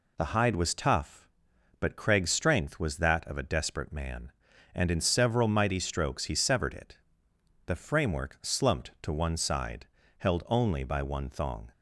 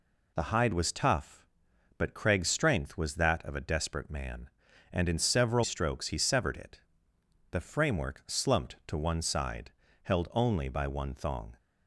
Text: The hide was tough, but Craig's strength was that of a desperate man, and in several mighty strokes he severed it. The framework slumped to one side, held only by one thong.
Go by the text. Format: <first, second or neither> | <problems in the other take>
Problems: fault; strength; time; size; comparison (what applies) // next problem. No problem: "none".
first | skips "mighty"; at 5.6 s